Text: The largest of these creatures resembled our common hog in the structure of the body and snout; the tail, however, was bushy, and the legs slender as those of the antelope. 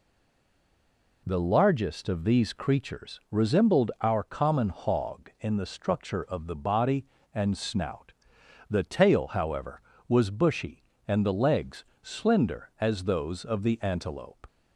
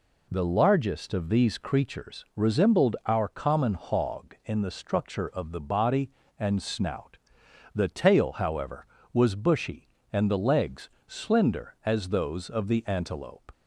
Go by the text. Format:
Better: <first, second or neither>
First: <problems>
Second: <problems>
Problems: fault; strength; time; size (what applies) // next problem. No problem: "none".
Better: second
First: stays silent before the first word; noticeable; until 1.2 s; 1.2 s long // pauses between "legs" and "slender"; slight; at 11.8 s; 0.16 s long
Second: pauses between "legs" and "slender"; slight; at 10.9 s; 0.16 s long